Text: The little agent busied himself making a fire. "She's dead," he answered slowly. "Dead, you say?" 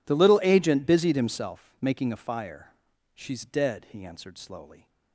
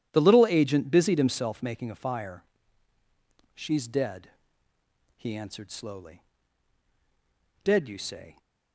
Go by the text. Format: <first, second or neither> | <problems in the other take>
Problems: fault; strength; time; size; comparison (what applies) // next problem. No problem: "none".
second | stops before "Dead you say"; at 4.8 s